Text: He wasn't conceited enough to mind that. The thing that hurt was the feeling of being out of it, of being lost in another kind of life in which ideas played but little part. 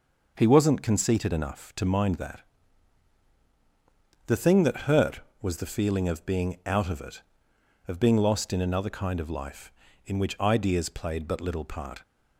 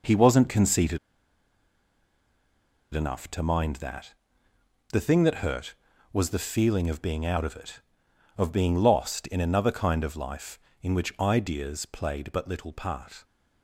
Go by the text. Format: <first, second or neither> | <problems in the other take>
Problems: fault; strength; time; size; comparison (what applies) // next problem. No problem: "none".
first | pauses between "conceited" and "enough"; strong; at 0.9 s; 1.9 s long